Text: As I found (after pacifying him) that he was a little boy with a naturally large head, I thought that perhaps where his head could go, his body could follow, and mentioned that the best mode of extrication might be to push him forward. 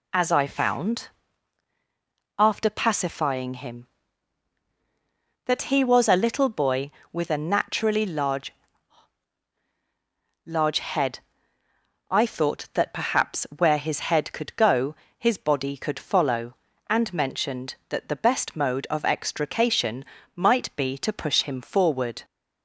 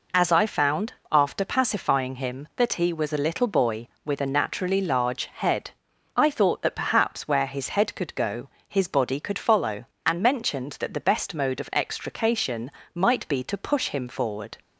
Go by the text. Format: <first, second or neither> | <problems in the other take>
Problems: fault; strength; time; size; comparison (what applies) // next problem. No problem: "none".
second | says "large" twice; at 10.4 s // pauses between "extrication" and "might"; slight; at 20.0 s; 0.32 s long; slight in the second